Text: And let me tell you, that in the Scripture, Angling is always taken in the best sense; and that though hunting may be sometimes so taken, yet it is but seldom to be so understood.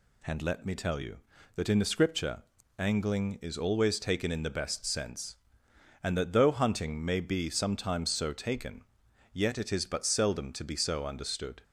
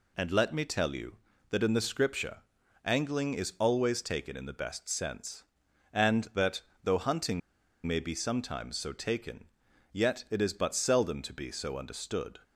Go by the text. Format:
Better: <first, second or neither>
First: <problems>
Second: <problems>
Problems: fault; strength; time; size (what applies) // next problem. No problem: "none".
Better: first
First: none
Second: pauses between "that" and "though"; slight; at 6.6 s; 0.22 s long // pauses between "hunting" and "may"; noticeable; at 7.4 s; 0.45 s long